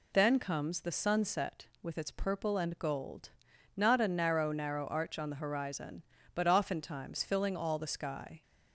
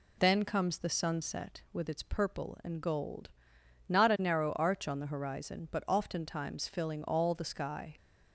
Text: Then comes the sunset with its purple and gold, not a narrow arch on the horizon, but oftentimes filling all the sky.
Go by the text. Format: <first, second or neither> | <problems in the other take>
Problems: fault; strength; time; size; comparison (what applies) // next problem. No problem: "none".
second | says "narrow" twice; at 4.5 s